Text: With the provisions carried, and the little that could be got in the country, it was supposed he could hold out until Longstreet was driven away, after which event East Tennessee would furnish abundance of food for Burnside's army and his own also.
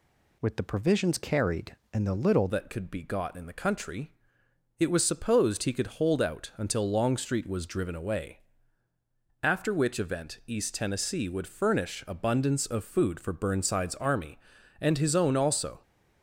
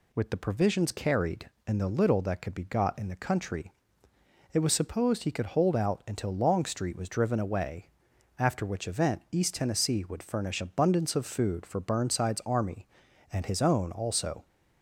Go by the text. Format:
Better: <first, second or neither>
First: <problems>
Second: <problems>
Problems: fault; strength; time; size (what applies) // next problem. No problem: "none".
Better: second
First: changes voice at "that"; from 2.4 s on; 13.4 s long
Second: none